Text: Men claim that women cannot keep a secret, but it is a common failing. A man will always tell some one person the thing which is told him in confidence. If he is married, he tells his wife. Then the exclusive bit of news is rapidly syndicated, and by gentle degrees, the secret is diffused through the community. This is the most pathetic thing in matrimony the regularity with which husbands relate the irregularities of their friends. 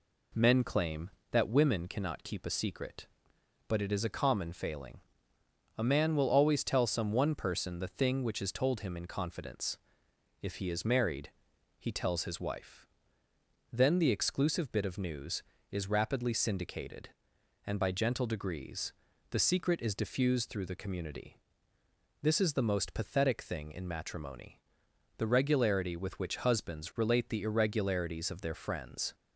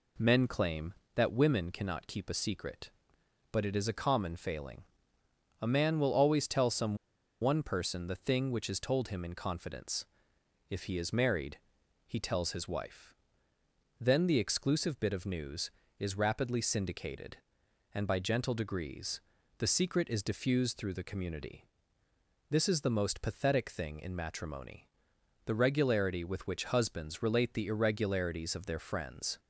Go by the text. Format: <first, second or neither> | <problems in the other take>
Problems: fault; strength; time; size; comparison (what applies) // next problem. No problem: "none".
first | pauses between "some" and "one"; noticeable; at 6.9 s; 0.46 s long // pauses between "matrimony" and "the"; noticeable; at 24.8 s; 0.60 s long; noticeable in the first